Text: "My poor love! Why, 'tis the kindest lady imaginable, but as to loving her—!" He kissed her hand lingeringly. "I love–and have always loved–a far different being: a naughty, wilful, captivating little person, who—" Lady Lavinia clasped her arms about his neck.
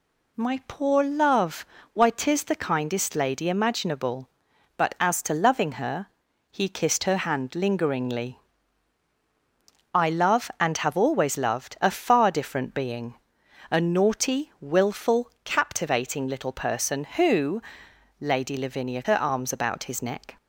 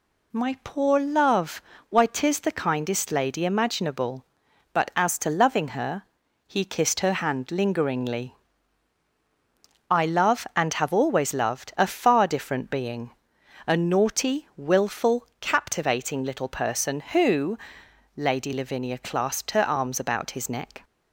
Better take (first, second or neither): second